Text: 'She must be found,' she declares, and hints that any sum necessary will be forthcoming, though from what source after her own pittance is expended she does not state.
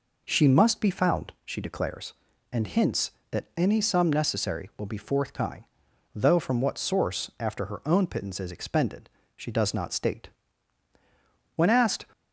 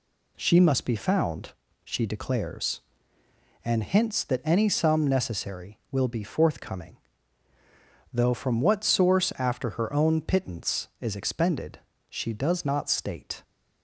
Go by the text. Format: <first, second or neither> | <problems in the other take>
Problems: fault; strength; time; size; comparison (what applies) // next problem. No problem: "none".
second | pauses between "expended" and "she"; slight; at 9.0 s; 0.26 s long; slight in the second // goes on to say "When asked"; from 11.5 s on; 0.50 s long